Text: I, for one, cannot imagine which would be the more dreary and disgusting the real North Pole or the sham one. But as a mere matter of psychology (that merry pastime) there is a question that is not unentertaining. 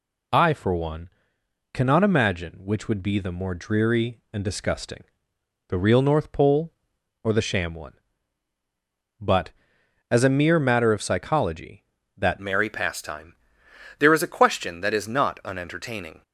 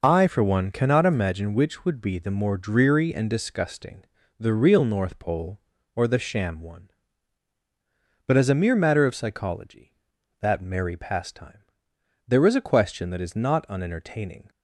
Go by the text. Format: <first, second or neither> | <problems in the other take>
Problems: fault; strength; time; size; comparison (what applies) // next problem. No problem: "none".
second | pauses between "disgusting" and "the"; noticeable; at 5.0 s; 0.64 s long; slight in the second // changes voice at "merry"; from 12.4 s on; 3.8 s long